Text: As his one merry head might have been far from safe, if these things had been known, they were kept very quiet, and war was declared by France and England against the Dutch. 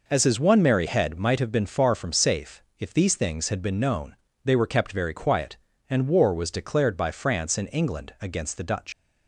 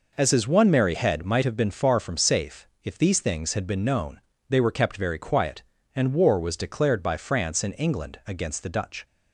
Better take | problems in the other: second | leaves "Dutch" unfinished; at 8.9 s; 70 ms

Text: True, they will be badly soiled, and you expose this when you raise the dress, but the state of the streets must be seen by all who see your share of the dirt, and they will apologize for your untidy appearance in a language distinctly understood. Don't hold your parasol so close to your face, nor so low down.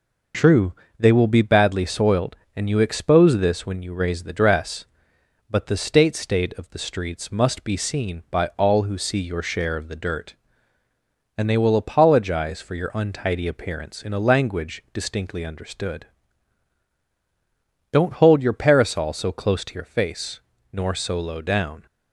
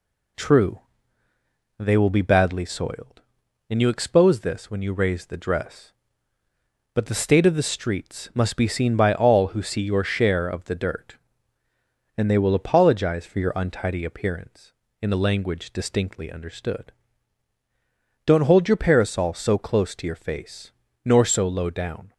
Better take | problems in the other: second | says "state" twice; at 6.1 s

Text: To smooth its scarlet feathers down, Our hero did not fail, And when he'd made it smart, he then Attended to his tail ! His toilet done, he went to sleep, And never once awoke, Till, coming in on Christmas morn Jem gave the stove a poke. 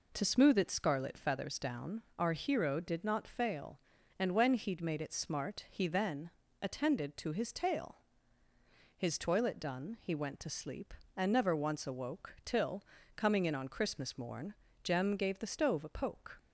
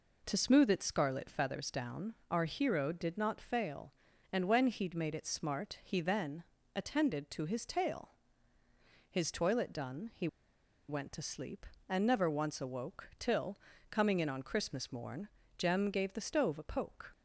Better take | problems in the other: first | pauses between "then" and "Attended"; slight; at 6.4 s; 0.32 s long; slight in the first // pauses between "he" and "went"; noticeable; at 10.2 s; 0.61 s long // pauses between "morn" and "Jem"; slight; at 15.2 s; 0.30 s long; slight in the first

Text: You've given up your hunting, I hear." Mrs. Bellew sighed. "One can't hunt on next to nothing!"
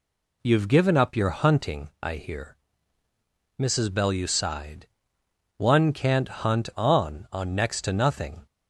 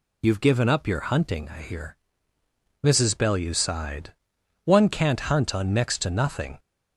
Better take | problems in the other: second | says "on" twice; at 7.2 s

